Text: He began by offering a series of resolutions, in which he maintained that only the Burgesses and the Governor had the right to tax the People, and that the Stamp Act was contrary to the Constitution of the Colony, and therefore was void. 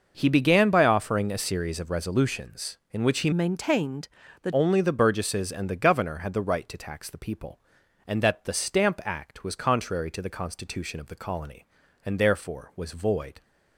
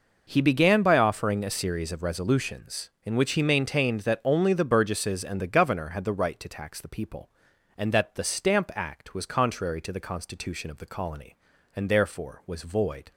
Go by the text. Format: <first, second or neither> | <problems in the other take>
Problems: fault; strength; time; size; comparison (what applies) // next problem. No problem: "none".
second | changes voice from "maintained" to "that"; from 3.3 to 4.5 s; 1.2 s long